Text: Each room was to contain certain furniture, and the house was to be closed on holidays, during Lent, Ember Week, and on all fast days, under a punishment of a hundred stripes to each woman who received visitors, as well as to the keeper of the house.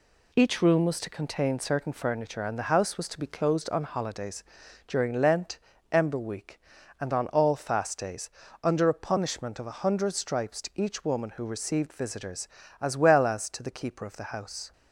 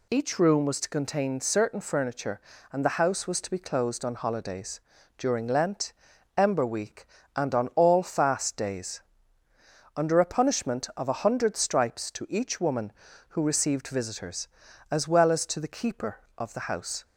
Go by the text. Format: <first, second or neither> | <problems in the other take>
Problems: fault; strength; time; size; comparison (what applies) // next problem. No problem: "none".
neither | none